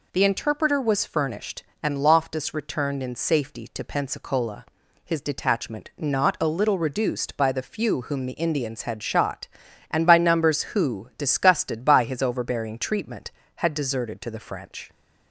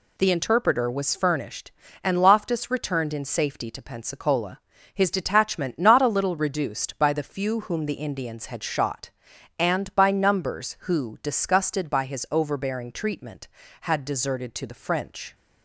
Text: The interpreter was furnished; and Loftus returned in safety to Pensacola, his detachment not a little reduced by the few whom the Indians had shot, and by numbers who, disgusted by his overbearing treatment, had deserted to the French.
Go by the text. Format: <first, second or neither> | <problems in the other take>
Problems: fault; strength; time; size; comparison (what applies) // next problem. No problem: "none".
neither | none